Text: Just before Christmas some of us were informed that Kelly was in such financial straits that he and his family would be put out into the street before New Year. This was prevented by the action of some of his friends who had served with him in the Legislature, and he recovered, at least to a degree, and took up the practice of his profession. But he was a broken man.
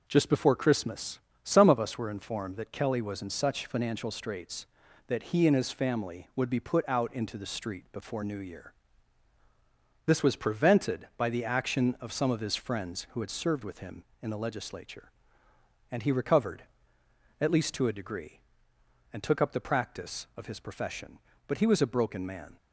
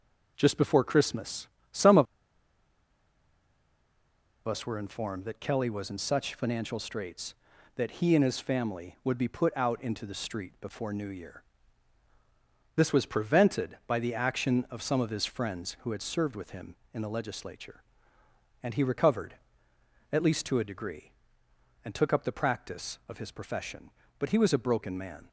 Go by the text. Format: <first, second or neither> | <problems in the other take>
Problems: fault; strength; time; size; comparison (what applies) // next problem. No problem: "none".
first | pauses between "Christmas" and "some"; slight; at 1.4 s; 0.24 s long; slight in the first // pauses between "of" and "us"; strong; at 2.0 s; 2.4 s long